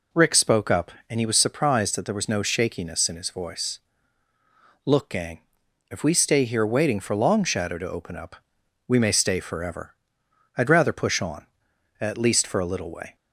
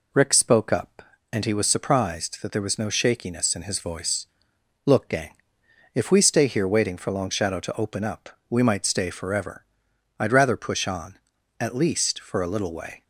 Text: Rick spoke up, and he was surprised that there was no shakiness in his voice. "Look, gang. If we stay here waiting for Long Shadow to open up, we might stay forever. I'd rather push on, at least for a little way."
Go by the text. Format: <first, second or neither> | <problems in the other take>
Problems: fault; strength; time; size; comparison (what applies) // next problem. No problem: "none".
second | says "may" for "might"; at 8.9 s